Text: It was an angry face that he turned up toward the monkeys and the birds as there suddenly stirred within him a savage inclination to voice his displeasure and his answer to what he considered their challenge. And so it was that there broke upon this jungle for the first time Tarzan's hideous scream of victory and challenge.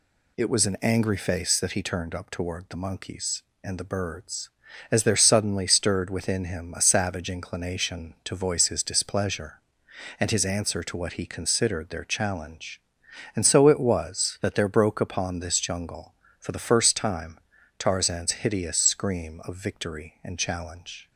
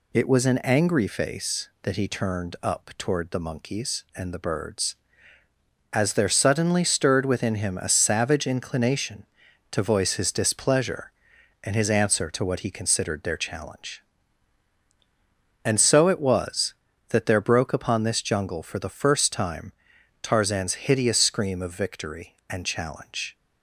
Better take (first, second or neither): neither